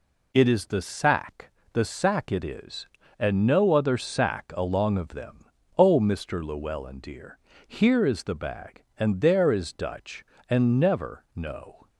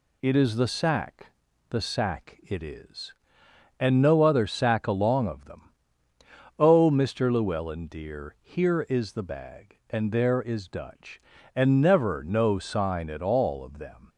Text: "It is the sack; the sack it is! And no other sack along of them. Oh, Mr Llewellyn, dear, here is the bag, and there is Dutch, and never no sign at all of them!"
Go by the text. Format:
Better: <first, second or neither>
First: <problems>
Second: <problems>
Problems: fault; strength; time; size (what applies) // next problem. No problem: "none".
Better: second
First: stops before "sign at all of them"; at 11.8 s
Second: none